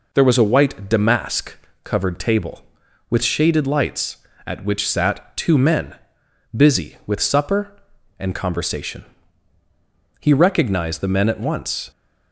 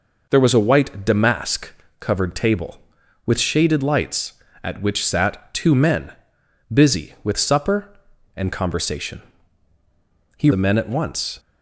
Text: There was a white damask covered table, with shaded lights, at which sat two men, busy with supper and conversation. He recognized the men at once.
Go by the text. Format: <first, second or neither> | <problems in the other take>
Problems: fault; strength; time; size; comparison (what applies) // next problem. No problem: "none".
first | pauses between "damask" and "covered"; slight; at 1.7 s; 0.26 s long; slight in the first // skips "recognized"; at 10.5 s